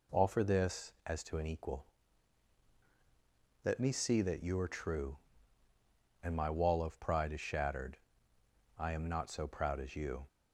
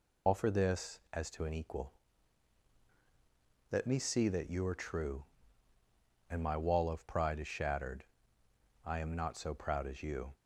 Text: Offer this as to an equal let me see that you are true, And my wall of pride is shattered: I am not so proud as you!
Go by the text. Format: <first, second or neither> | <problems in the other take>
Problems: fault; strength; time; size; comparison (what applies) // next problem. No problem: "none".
first | loses the start of "Offer"; at 0.2 s; 90 ms // pauses between "equal" and "let"; strong; at 1.9 s; 1.7 s long; strong in the first